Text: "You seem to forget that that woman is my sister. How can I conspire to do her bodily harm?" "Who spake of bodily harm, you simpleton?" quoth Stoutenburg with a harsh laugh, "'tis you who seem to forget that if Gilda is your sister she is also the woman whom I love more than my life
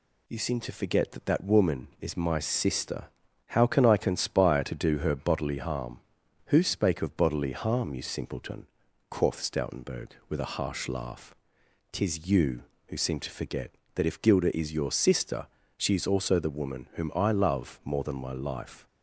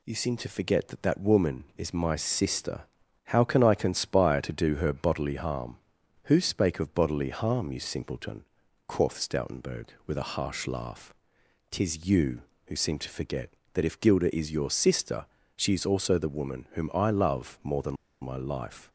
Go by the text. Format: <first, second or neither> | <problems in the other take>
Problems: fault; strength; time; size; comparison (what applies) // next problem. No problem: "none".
first | pauses between "sister" and "she"; slight; at 15.2 s; 0.30 s long; slight in the first // pauses between "than" and "my"; slight; at 17.9 s; 0.26 s long